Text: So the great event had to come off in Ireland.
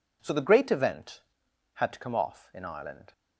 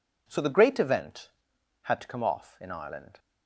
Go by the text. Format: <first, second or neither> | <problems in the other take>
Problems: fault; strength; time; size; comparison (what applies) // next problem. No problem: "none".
neither | none